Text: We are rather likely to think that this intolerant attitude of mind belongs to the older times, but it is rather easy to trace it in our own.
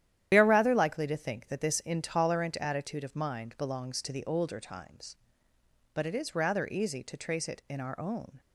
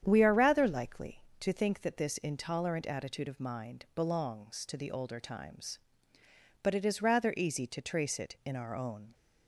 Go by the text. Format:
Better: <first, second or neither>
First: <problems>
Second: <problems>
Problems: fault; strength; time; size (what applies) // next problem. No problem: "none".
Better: second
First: loses the start of "We"; at 0.3 s; 50 ms // starts louder than the rest; strong; until 1.3 s; 11 dB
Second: starts louder than the rest; strong; until 1.0 s; 9 dB